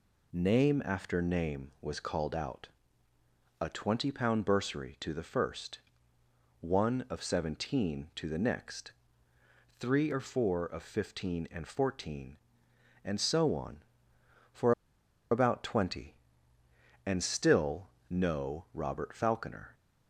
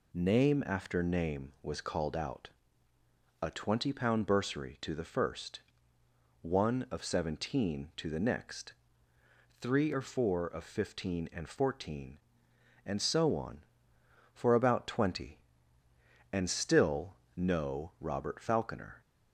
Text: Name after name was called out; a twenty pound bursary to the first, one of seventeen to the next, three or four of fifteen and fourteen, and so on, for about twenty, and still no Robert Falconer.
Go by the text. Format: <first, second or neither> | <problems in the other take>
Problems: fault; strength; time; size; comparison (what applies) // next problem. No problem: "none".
second | pauses between "for" and "about"; noticeable; at 14.7 s; 0.58 s long // pauses between "still" and "no"; slight; at 17.8 s; 0.18 s long; slight in the second